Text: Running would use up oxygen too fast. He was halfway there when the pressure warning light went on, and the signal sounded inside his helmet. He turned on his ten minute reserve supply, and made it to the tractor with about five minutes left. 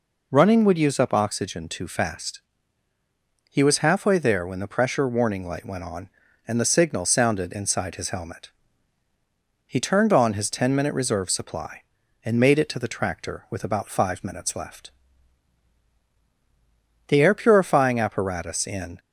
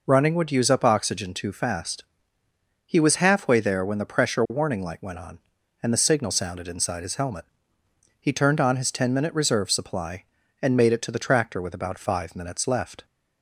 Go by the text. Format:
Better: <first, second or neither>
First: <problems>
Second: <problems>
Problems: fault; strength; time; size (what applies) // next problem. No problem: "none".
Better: second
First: goes on to say "The air purifying apparatus in"; strong; from 17.0 s on; 1.9 s long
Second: none